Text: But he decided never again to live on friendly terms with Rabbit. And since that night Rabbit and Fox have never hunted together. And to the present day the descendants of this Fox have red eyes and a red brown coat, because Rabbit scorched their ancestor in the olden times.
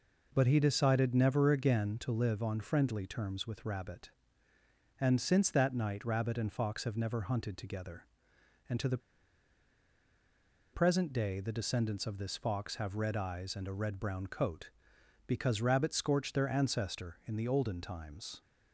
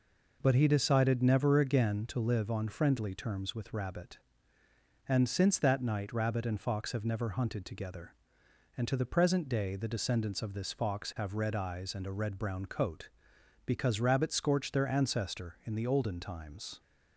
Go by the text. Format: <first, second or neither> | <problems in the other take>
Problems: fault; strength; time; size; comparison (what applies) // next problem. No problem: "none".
second | pauses between "the" and "present"; strong; at 8.9 s; 1.7 s long